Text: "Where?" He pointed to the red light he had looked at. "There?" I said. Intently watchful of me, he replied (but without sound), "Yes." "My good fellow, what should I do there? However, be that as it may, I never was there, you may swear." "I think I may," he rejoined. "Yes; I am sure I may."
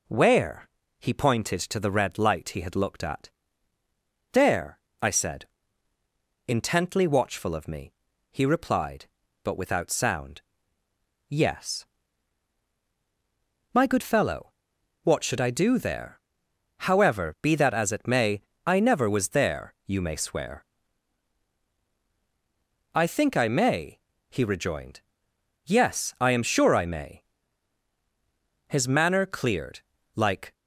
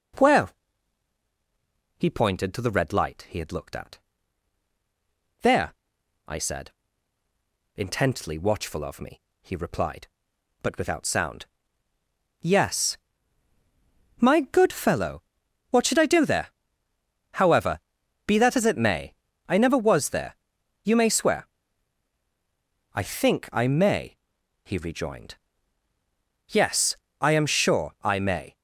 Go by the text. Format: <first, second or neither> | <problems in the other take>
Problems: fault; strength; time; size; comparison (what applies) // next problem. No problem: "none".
second | goes on to say "His manner cleared like"; strong; from 28.6 s on; 1.8 s long